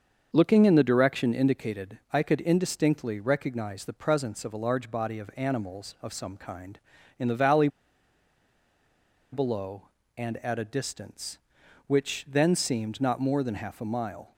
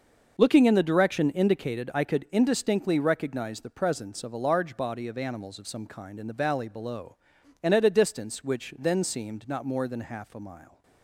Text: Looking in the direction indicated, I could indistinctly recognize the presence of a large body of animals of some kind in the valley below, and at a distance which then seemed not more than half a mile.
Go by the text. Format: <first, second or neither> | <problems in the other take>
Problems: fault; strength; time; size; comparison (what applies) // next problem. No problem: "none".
second | starts louder than the rest; until 1.3 s; 6.5 dB // pauses between "valley" and "below"; strong; at 7.6 s; 1.6 s long